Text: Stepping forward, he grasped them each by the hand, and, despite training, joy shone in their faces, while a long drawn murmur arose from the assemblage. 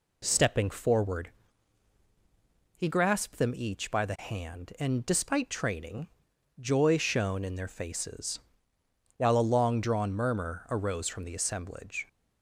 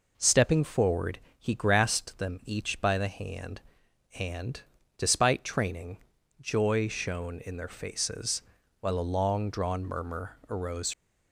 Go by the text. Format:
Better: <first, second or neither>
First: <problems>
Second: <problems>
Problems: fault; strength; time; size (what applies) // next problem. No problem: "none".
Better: first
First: none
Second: stops before "from the assemblage"; at 10.9 s